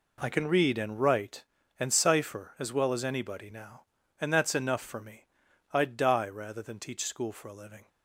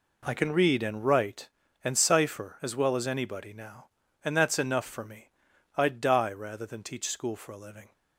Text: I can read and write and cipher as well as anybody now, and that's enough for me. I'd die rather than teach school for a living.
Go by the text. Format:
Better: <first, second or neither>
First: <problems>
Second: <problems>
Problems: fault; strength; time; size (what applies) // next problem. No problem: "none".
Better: neither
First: none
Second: none